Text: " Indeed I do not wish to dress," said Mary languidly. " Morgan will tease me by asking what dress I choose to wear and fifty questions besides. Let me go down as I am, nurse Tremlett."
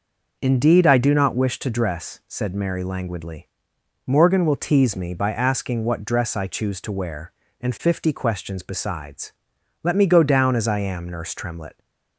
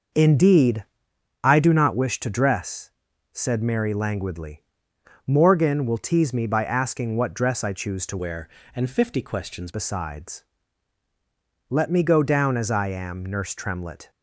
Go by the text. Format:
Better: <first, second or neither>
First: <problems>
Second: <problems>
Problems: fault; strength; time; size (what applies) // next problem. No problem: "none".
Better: first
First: none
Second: starts louder than the rest; noticeable; until 1.7 s; 6 dB // pauses between "Indeed" and "I"; noticeable; at 0.8 s; 0.56 s long // changes voice from "wear" to "questions"; from 8.1 to 9.6 s; 1.5 s long